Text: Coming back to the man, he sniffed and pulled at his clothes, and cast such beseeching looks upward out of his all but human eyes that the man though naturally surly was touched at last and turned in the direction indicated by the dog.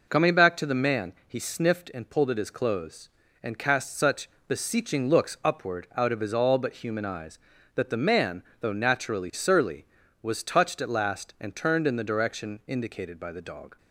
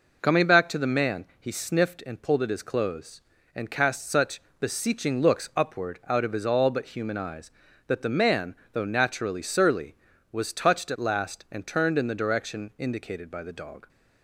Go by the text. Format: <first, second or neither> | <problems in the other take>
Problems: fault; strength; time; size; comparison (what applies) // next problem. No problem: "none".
neither | pauses between "such" and "beseeching"; slight; the same in both // pauses between "man" and "though"; slight; the same in both